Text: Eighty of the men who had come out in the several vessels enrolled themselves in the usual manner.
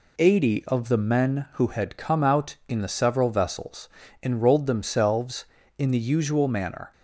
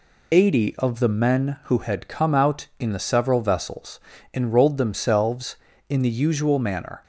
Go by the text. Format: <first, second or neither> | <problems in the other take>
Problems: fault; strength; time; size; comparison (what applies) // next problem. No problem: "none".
first | loses the start of "Eighty"; at 0.3 s; 30 ms // pauses between "vessels" and "enrolled"; slight; at 3.9 s; 0.34 s long; slight in the first